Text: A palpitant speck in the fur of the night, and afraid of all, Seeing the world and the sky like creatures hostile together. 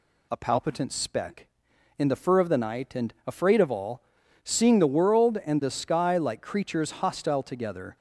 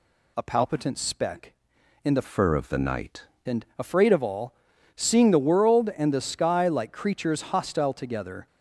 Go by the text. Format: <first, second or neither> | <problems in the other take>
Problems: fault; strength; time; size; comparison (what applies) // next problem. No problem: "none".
first | changes voice from "fur" to "night"; from 2.2 to 3.2 s; 1.0 s long